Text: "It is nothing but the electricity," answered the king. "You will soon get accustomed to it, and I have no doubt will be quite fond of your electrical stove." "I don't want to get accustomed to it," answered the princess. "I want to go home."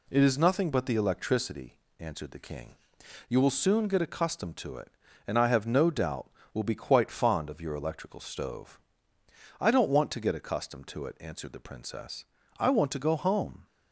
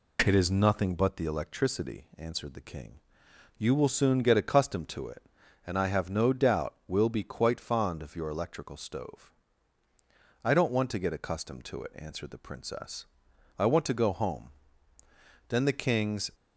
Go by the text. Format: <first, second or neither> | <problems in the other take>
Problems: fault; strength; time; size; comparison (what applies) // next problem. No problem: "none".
first | goes on to say "Then the king's"; noticeable; from 15.4 s on; 0.82 s long